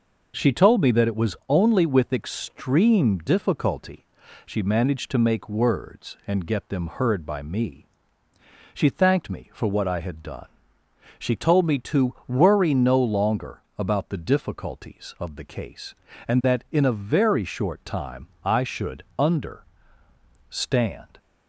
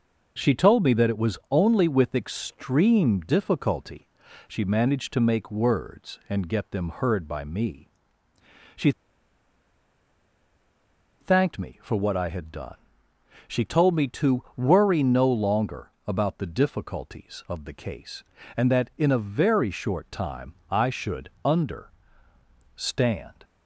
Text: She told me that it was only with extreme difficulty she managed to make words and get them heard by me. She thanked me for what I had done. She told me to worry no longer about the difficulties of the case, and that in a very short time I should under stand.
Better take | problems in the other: first | pauses between "difficulty" and "she"; at 4.0 s; 0.40 s long; also in the first // pauses between "She" and "thanked"; strong; at 8.9 s; 2.2 s long // pauses between "longer" and "about"; slight; at 15.8 s; 0.18 s long; slight in the first // pauses between "time" and "I"; slight; at 20.5 s; 0.16 s long; slight in the first // pauses between "should" and "under"; slight; at 21.2 s; 0.16 s long; slight in the first // pauses between "under" and "stand"; noticeable; at 21.8 s; 0.86 s long; noticeable in the first

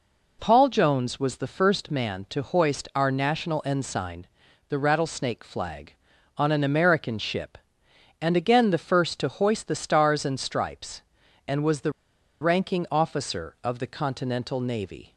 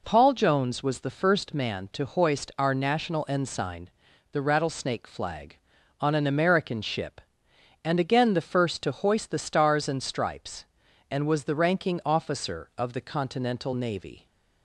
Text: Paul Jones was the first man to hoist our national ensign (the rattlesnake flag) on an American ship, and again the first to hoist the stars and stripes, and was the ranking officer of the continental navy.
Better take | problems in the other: second | pauses between "the" and "ranking"; noticeable; at 11.9 s; 0.49 s long

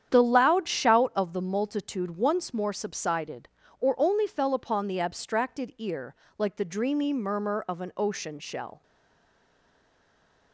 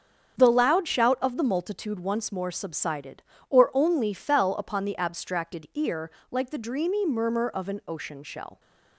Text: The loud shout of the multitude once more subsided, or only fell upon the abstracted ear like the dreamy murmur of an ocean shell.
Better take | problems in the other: second | starts louder than the rest; strong; until 1.1 s; 9 dB; strong in the second // pauses between "ear" and "like"; slight; at 6.1 s; 0.20 s long; slight in the second // stays silent after the last word; noticeable; from 8.8 s on; 1.7 s long

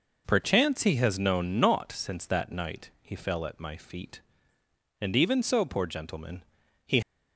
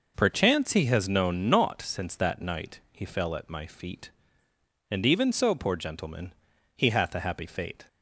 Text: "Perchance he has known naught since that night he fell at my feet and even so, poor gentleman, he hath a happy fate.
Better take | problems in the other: second | stops before "hath a happy fate"; at 7.0 s

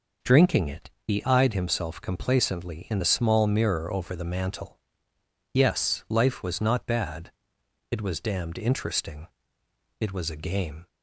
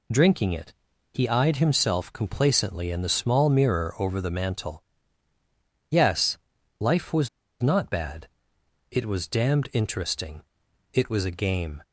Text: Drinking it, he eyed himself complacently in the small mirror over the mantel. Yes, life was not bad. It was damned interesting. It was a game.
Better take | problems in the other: first | pauses between "was" and "not"; slight; at 7.2 s; 0.34 s long

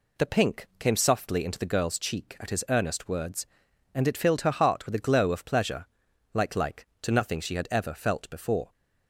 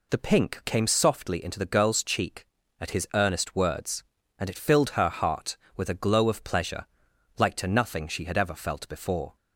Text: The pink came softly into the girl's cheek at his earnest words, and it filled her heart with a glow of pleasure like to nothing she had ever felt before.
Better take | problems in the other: second | pauses between "pleasure" and "like"; noticeable; at 5.8 s; 0.48 s long; noticeable in the second // says "like" twice; at 6.5 s

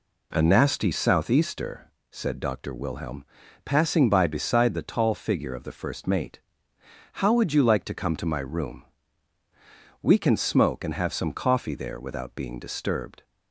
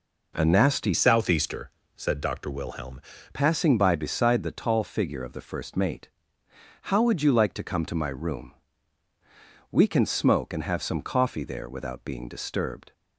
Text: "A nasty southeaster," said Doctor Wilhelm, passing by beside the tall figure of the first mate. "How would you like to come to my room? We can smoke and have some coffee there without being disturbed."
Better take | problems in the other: first | changes voice from "southeaster" to "Wilhelm"; from 0.9 to 2.9 s; 2.0 s long

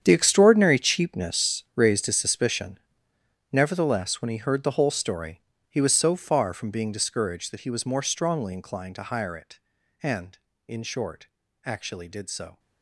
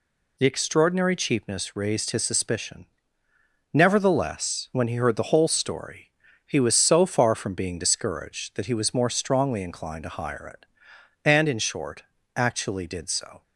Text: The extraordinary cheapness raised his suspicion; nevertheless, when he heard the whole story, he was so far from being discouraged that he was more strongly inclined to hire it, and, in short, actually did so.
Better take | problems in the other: second | gets quieter; strong; throughout; 15 dB

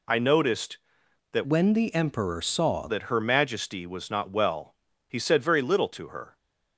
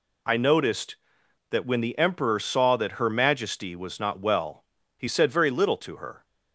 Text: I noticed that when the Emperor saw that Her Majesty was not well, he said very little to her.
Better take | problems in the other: second | changes voice from "when" to "saw"; from 1.4 to 2.8 s; 1.4 s long

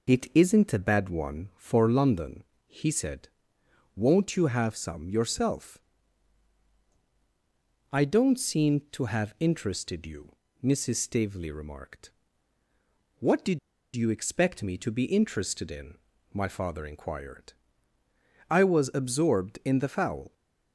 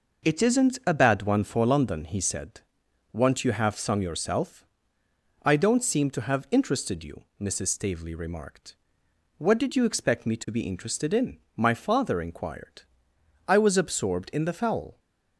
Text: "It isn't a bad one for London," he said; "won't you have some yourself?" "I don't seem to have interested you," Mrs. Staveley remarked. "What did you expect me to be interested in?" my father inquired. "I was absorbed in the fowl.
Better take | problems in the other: second | pauses between "did" and "you"; slight; at 13.5 s; 0.36 s long

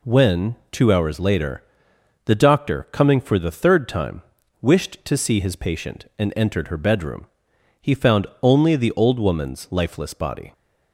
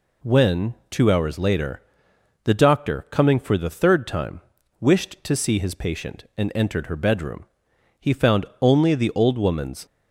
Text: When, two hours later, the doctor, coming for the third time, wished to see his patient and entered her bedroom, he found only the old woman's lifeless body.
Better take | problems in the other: first | pauses between "found" and "only"; slight; at 8.4 s; 0.16 s long; slight in the first // stops before "lifeless body"; at 9.8 s

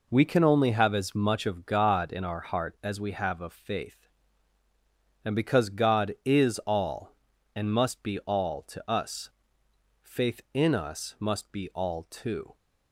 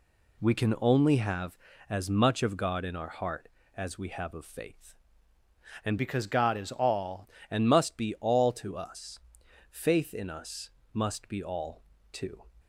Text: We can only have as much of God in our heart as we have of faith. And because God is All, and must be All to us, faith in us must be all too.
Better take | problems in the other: first | changes voice from "because" to "All"; from 5.9 to 7.2 s; 1.3 s long // pauses between "us" and "must"; slight; at 10.6 s; 0.24 s long // pauses between "all" and "too"; slight; at 11.8 s; 0.32 s long

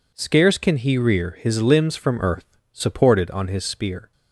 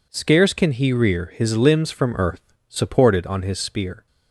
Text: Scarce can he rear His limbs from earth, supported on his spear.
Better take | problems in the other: neither | none

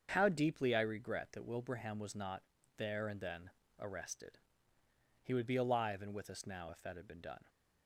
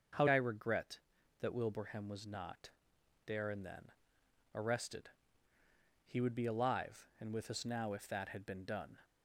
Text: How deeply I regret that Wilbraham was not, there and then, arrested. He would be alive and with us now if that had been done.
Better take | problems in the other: first | starts louder than the rest; until 1.5 s; 6.5 dB; also in the first // skips "deeply"; at 0.2 s

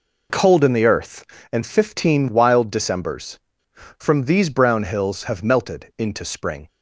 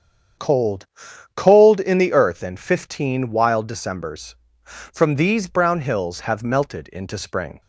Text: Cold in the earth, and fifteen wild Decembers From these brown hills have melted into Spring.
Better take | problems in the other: first | starts louder than the rest; strong; until 1.8 s; 8 dB // says "Cold" twice; at 1.3 s

